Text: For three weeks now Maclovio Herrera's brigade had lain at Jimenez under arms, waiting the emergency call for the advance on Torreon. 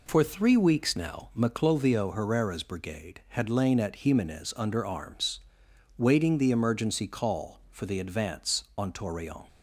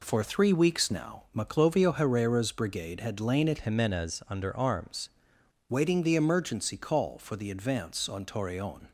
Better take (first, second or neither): first